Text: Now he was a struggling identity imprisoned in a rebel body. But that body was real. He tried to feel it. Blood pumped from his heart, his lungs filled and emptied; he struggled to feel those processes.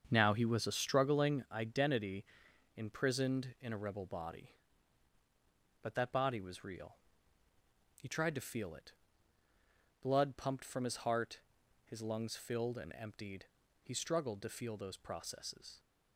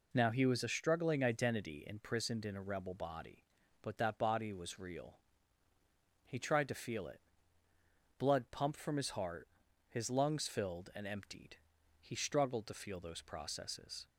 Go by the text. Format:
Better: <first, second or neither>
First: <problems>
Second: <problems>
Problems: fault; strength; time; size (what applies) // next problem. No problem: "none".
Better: second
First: starts louder than the rest; until 1.5 s; 7 dB // pauses between "identity" and "imprisoned"; noticeable; at 2.2 s; 0.52 s long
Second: none